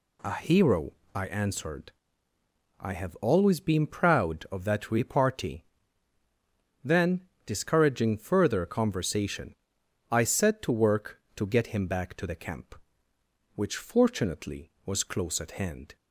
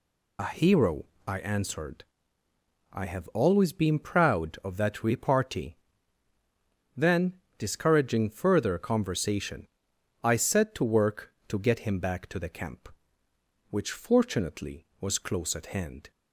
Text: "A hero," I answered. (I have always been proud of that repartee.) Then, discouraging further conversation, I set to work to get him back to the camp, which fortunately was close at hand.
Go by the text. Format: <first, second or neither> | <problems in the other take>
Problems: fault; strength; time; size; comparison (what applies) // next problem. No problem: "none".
first | loses the start of "A"; at 0.3 s; 75 ms